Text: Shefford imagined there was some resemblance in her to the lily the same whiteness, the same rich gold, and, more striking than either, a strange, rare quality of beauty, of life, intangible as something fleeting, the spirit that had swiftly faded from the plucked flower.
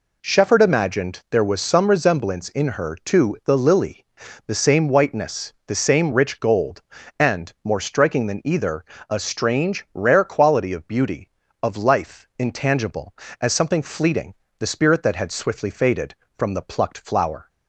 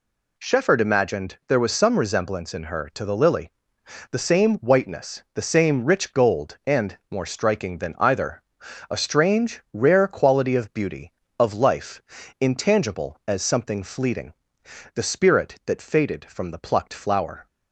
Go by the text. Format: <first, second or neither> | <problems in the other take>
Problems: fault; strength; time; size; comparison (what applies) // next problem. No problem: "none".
first | pauses between "lily" and "the"; noticeable; at 3.5 s; 0.58 s long; also in the first // skips "had swiftly"; at 15.8 s